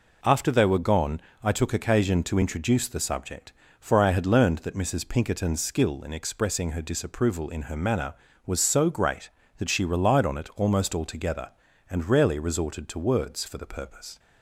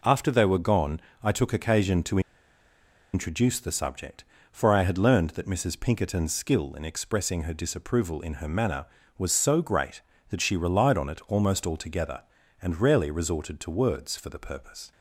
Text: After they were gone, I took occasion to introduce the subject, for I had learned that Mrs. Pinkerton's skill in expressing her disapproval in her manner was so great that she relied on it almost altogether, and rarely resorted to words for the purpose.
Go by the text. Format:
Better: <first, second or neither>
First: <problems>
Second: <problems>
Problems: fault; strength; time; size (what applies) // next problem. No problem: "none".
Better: first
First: none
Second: pauses between "to" and "introduce"; noticeable; at 2.1 s; 0.93 s long